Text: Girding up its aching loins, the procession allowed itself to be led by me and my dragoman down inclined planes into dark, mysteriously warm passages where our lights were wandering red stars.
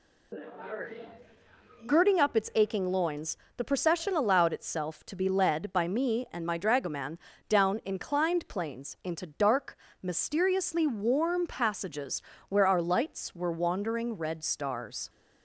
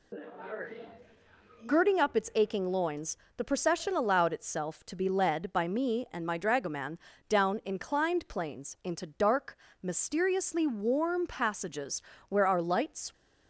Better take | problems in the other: first | pauses between "dragoman" and "down"; slight; at 6.9 s; 0.32 s long; slight in the first // pauses between "passages" and "where"; slight; at 12.0 s; 0.26 s long; slight in the first // stops before "were wandering red stars"; at 13.1 s

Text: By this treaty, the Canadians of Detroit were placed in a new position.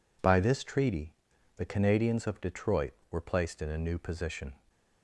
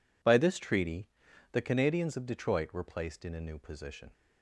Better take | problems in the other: neither | none

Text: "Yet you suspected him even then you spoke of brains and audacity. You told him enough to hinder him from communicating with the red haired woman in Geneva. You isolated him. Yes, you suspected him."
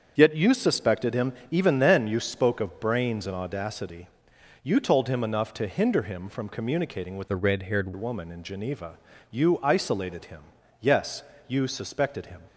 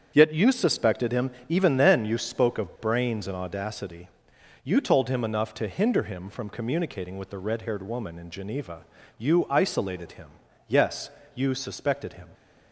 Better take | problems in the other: second | starts louder than the rest; until 1.1 s; 7 dB; strong in the second // pauses between "him" and "even"; slight; at 1.3 s; 0.16 s long; slight in the second // changes voice from "the" to "haired"; from 7.2 to 7.9 s; 0.7 s long

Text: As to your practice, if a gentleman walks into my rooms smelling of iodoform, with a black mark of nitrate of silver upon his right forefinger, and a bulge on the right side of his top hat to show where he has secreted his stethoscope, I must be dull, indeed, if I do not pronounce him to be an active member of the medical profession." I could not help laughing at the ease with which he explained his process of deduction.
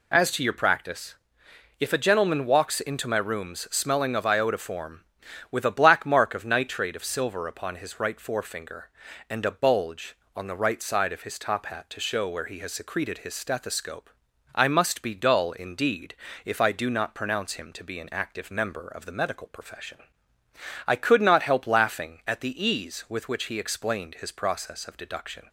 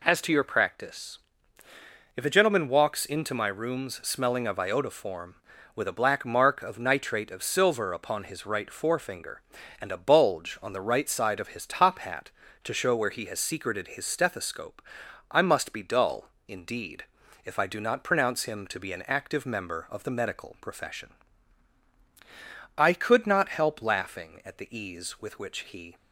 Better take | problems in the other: first | stops before "explained his process of deduction"; at 25.9 s

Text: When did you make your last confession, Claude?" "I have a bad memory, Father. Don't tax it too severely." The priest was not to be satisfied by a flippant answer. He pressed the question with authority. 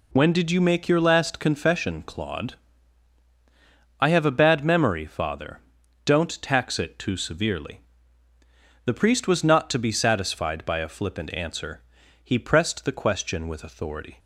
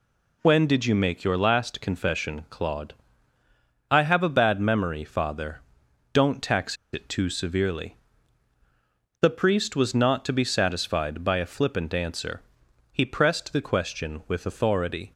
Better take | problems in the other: first | pauses between "tax" and "it"; slight; at 6.7 s; 0.17 s long

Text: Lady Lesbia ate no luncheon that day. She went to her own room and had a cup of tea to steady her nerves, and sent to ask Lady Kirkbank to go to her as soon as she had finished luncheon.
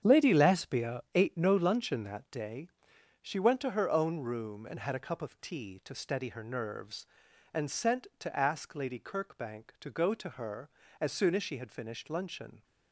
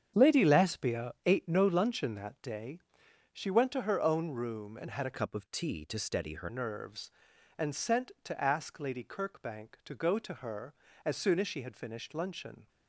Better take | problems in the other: first | starts louder than the rest; strong; until 1.3 s; 8 dB; strong in the first // changes voice from "cup" to "her"; from 5.1 to 6.4 s; 1.3 s long

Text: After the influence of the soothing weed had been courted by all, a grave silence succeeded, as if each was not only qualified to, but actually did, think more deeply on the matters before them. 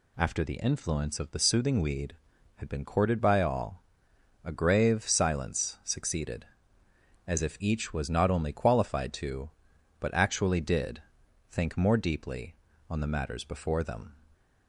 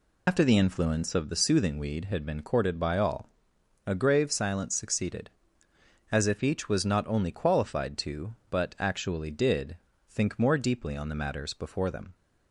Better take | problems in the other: first | loses the start of "After"; at 0.2 s; 100 ms

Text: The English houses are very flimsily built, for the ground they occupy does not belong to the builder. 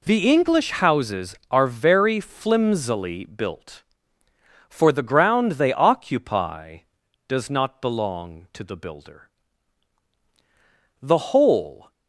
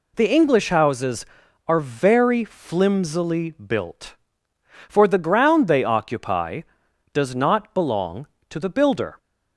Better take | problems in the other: second | goes on to say "The whole"; noticeable; from 11.0 s on; 0.90 s long

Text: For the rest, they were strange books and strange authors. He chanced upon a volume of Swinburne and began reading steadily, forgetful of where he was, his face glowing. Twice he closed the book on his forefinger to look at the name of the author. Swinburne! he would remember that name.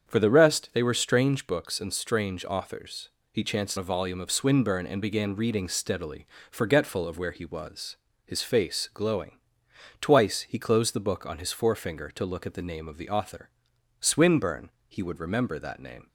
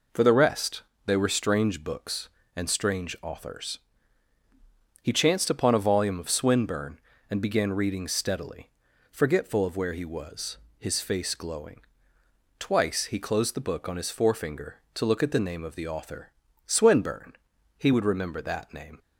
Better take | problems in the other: second | starts louder than the rest; strong; until 1.1 s; 7.5 dB // skips "upon"; at 3.7 s

